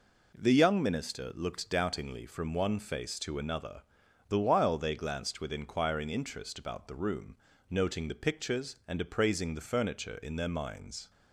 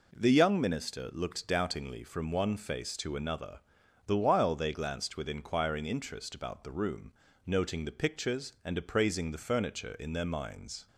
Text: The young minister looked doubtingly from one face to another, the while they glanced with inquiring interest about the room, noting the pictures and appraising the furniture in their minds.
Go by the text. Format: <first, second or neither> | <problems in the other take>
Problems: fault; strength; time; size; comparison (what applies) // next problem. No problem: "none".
neither | none